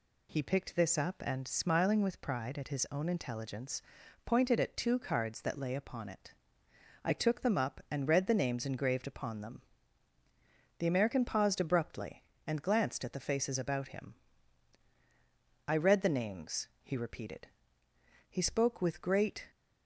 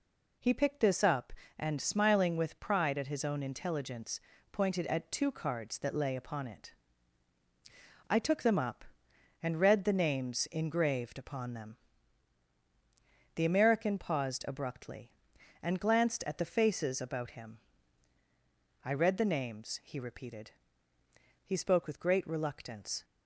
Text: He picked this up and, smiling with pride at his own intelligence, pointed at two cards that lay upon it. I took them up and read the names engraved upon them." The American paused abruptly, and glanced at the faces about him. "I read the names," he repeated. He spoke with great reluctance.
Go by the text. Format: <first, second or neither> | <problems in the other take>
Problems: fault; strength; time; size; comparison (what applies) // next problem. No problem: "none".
second | stops before "reluctance"; at 19.5 s